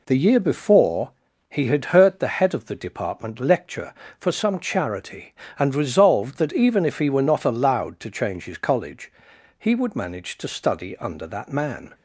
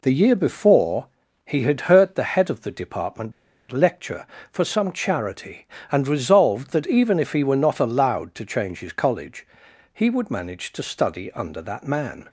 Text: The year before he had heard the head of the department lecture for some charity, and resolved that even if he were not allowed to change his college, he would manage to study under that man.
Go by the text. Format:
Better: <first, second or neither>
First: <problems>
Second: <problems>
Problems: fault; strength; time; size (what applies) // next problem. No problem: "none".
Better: first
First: pauses between "before" and "he"; at 1.1 s; 0.40 s long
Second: pauses between "before" and "he"; at 1.0 s; 0.40 s long // pauses between "department" and "lecture"; at 3.3 s; 0.39 s long